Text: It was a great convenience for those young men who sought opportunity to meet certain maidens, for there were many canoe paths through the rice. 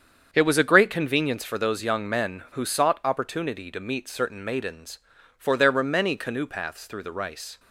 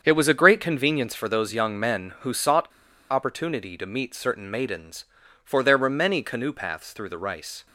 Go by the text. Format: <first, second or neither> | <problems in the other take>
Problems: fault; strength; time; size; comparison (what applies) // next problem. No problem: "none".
first | starts louder than the rest; strong; until 1.0 s; 7.5 dB; strong in the first // pauses between "sought" and "opportunity"; at 2.6 s; 0.42 s long